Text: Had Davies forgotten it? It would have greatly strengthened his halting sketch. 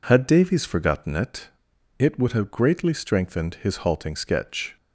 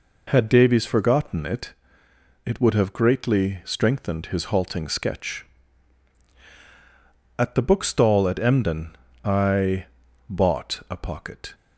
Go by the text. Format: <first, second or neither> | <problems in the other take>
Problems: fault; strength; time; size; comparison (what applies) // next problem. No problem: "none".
first | goes on to say "At the bookstall at Emden I bought a pocket"; strong; from 7.3 s on; 4.1 s long